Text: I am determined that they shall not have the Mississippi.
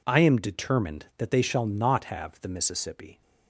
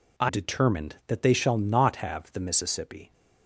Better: first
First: none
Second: skips "am"; at 0.2 s

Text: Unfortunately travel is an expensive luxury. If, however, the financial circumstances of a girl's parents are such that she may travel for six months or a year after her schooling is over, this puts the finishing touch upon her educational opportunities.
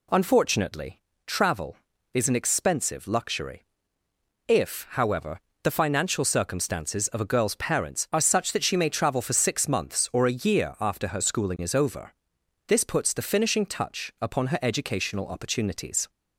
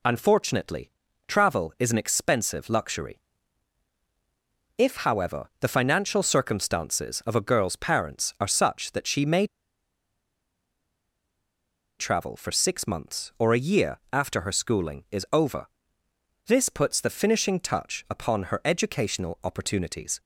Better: first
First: pauses between "Unfortunately" and "travel"; slight; at 0.9 s; 0.28 s long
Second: pauses between "Unfortunately" and "travel"; slight; at 0.9 s; 0.36 s long // pauses between "may" and "travel"; strong; at 9.4 s; 2.5 s long

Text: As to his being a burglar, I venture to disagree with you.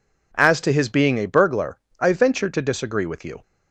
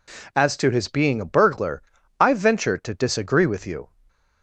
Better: neither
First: none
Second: none

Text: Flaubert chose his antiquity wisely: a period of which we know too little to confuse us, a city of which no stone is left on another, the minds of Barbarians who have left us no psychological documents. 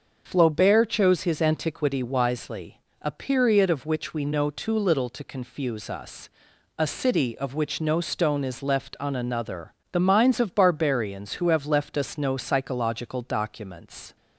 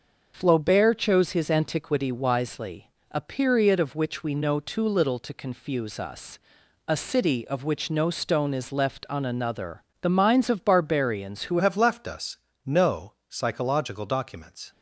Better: first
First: starts louder than the rest; until 1.2 s; 6.5 dB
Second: starts louder than the rest; until 1.3 s; 6.5 dB // changes voice at "have"; from 11.5 s on; 3.2 s long // pauses between "us" and "no"; slight; at 12.3 s; 0.28 s long

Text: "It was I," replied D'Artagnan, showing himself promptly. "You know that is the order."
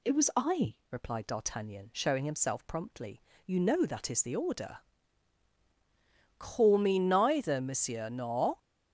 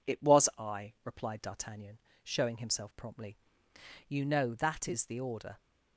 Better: second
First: goes on to say "Call me neither monsieur nor"; strong; from 6.4 s on; 2.1 s long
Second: none

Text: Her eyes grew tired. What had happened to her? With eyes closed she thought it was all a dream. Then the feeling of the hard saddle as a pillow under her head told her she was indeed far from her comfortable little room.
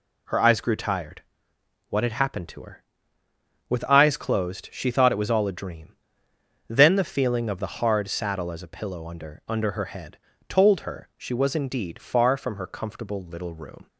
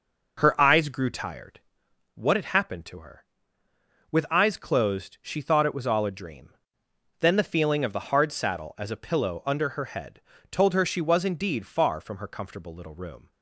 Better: second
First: says "under" twice; at 9.4 s // pauses between "head" and "told"; slight; at 10.1 s; 0.32 s long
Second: pauses between "head" and "told"; slight; at 10.2 s; 0.32 s long

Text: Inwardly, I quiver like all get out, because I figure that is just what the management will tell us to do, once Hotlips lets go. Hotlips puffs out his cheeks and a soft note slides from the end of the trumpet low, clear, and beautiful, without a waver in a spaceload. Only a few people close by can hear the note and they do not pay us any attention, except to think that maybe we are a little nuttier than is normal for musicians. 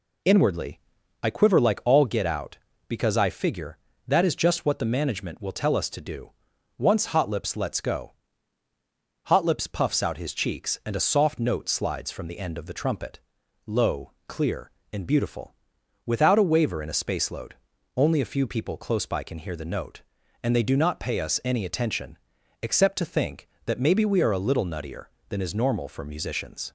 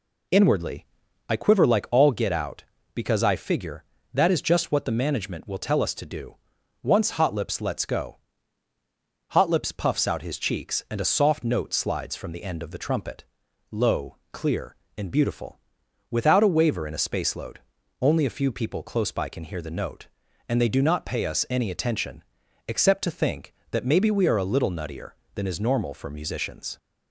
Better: neither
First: pauses between "trumpet" and "low"; noticeable; at 13.1 s; 0.48 s long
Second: pauses between "trumpet" and "low"; noticeable; at 13.2 s; 0.48 s long

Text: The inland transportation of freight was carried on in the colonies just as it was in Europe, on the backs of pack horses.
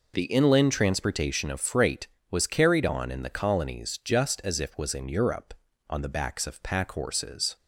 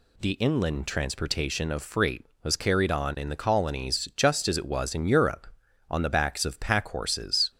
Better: second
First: says "if" for "it"; at 4.6 s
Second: none

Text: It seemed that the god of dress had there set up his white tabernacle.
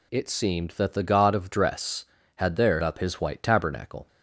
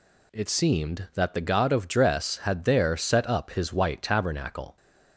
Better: second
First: skips "set"; at 2.8 s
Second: none

